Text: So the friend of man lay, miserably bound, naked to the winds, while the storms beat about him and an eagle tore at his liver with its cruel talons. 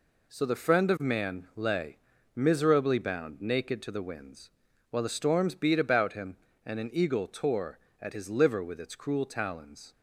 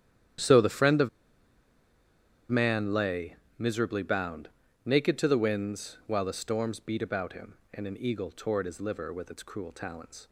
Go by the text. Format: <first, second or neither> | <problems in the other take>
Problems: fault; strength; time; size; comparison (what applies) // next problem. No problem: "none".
first | starts louder than the rest; strong; until 2.8 s; 10.5 dB // pauses between "of" and "man"; strong; at 1.0 s; 1.4 s long